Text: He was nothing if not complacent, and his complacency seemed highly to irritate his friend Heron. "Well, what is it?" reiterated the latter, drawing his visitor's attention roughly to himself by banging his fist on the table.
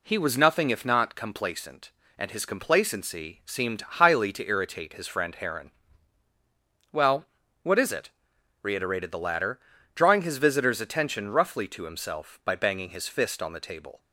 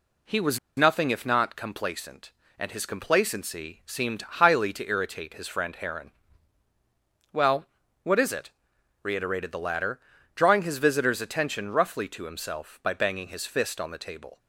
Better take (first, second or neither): first